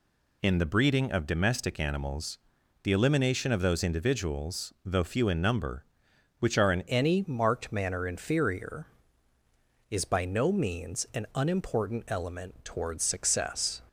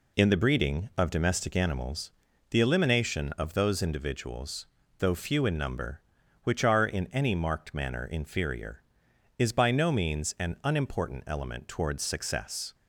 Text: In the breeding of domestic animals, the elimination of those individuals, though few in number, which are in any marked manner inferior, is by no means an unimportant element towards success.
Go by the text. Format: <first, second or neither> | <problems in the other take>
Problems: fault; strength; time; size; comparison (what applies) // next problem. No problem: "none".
second | changes voice at "any"; from 6.8 s on; 7.0 s long